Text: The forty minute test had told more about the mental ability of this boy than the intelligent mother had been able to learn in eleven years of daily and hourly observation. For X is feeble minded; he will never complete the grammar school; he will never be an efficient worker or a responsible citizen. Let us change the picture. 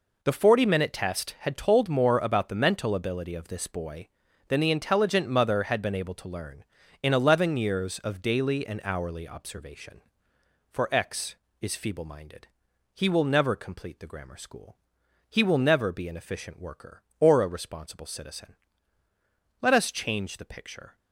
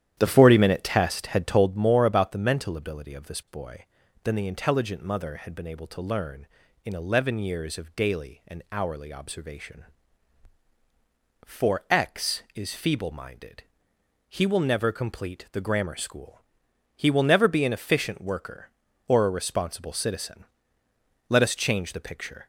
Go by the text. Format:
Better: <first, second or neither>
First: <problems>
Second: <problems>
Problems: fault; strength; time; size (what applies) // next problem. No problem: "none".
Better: first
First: none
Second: starts louder than the rest; strong; until 1.8 s; 11 dB